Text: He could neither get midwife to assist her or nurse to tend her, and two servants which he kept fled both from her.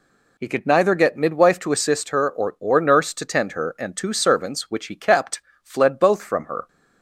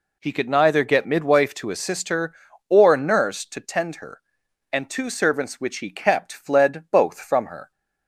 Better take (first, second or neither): second